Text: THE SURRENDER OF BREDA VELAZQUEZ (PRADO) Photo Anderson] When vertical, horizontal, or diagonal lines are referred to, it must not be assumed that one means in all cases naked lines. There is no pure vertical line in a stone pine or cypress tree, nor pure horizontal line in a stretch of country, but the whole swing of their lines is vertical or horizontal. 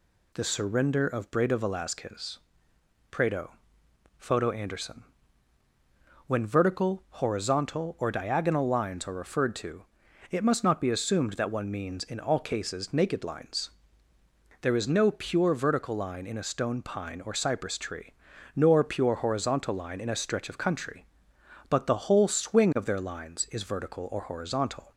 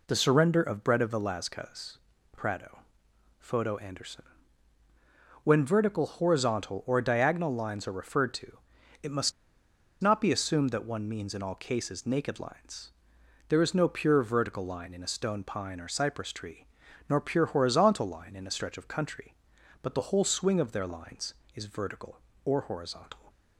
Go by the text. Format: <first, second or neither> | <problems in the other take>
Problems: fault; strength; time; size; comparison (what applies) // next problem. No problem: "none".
first | pauses between "Anderson" and "When"; at 4.2 s; 1.1 s long; also in the first // pauses between "must" and "not"; noticeable; at 9.3 s; 0.68 s long